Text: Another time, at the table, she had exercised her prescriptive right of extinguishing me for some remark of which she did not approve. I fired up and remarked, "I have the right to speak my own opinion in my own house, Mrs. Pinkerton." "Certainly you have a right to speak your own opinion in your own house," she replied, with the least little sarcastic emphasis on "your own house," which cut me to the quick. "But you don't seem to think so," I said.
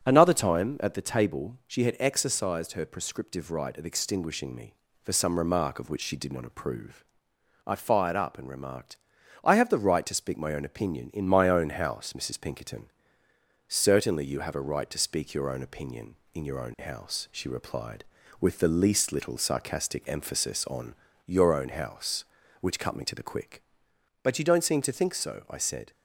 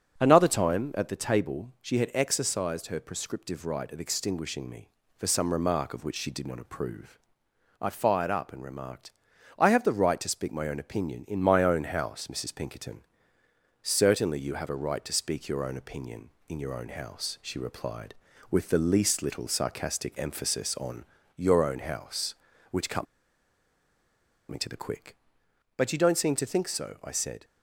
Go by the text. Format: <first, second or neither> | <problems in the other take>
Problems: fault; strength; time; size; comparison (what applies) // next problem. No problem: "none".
first | starts louder than the rest; until 1.2 s; 7 dB; also in the first // pauses between "on" and "your"; slight; at 21.0 s; 0.30 s long; slight in the first // pauses between "cut" and "me"; strong; at 23.0 s; 1.4 s long